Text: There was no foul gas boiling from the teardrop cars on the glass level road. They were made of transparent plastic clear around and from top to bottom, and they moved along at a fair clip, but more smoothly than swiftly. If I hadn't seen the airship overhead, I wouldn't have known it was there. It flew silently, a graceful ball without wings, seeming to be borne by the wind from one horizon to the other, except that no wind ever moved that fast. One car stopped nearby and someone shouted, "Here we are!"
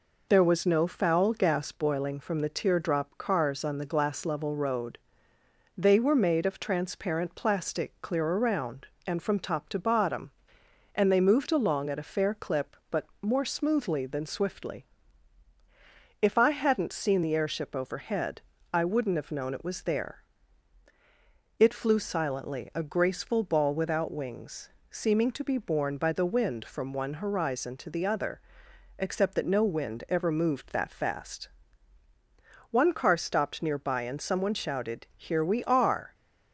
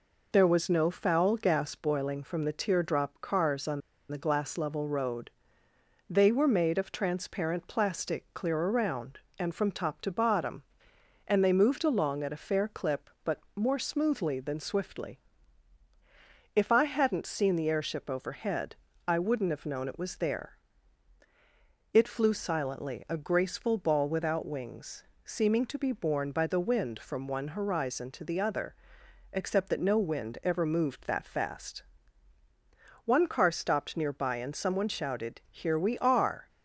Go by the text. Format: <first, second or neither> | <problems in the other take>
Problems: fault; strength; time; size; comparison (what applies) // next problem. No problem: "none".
first | pauses between "on" and "the"; slight; at 3.8 s; 0.29 s long // pauses between "but" and "more"; slight; at 13.3 s; 0.16 s long; slight in the first